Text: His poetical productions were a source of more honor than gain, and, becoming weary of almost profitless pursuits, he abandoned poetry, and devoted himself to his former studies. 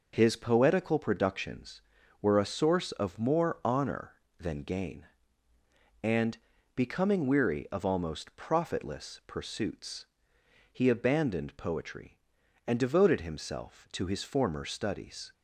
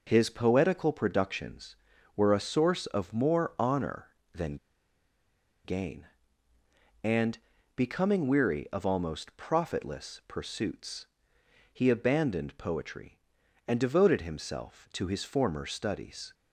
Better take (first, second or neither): first